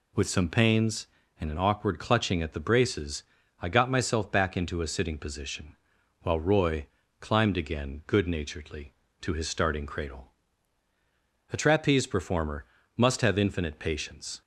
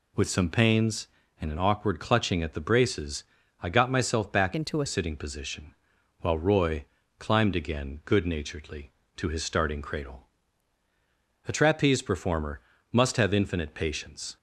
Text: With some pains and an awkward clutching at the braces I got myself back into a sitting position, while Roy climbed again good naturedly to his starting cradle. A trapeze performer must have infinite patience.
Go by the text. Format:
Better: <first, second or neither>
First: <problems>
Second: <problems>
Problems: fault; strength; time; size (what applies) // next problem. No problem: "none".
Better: first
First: pauses between "braces" and "I"; slight; at 3.2 s; 0.36 s long // pauses between "Roy" and "climbed"; slight; at 6.8 s; 0.34 s long // pauses between "performer" and "must"; slight; at 12.6 s; 0.30 s long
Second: pauses between "braces" and "I"; slight; at 3.2 s; 0.36 s long // changes voice from "into" to "a"; from 4.5 to 4.8 s; 0.3 s long // pauses between "Roy" and "climbed"; slight; at 6.8 s; 0.34 s long // pauses between "performer" and "must"; slight; at 12.6 s; 0.30 s long